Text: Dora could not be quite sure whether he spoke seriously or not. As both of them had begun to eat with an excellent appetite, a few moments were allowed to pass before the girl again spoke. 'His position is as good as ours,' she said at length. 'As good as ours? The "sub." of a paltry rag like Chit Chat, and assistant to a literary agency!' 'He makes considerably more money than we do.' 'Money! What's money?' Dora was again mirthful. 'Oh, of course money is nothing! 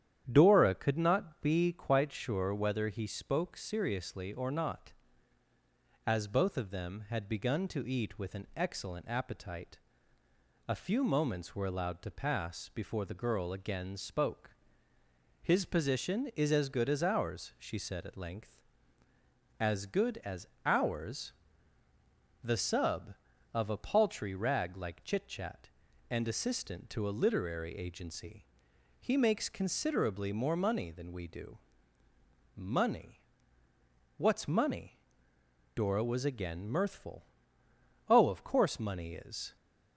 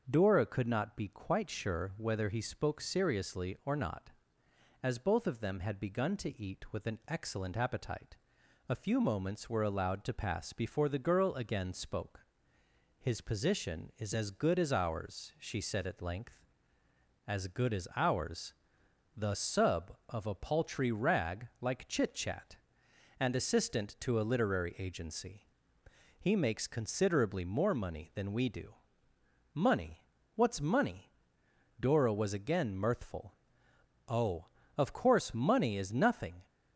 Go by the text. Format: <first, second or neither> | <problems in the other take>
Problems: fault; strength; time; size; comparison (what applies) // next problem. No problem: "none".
second | starts louder than the rest; strong; until 1.3 s; 10 dB; also in the second // pauses between "as" and "ours"; slight; at 20.4 s; 0.16 s long // stops before "nothing"; at 39.5 s